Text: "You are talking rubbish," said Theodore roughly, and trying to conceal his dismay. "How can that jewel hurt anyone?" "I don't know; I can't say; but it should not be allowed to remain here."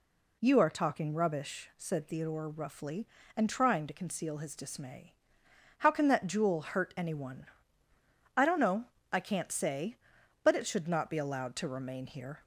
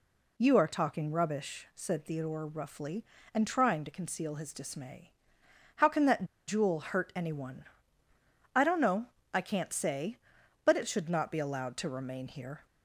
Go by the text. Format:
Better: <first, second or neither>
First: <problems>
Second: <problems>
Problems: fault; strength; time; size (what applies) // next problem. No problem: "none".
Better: first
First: none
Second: pauses between "that" and "jewel"; slight; at 6.2 s; 0.23 s long